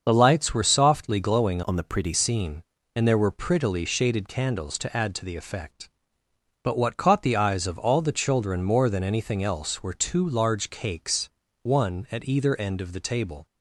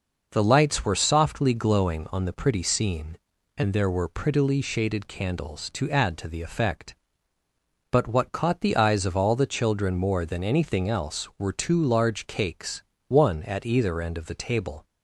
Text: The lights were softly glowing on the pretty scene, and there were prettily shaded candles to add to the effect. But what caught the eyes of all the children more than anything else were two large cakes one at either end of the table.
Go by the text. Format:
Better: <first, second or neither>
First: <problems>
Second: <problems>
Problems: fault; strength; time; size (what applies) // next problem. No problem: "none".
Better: second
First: starts louder than the rest; until 1.0 s; 6.5 dB // changes voice from "on" to "pretty"; from 1.6 to 2.1 s; 0.5 s long // pauses between "cakes" and "one"; slight; at 11.2 s; 0.32 s long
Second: pauses between "cakes" and "one"; slight; at 12.8 s; 0.24 s long